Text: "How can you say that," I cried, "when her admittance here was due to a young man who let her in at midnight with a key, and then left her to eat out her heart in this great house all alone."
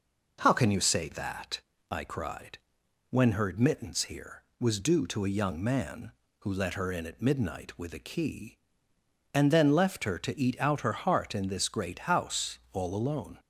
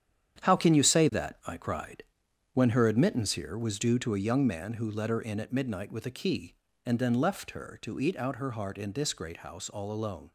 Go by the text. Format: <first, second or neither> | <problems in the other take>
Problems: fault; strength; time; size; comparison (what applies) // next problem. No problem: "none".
first | gets quieter; strong; throughout; 9 dB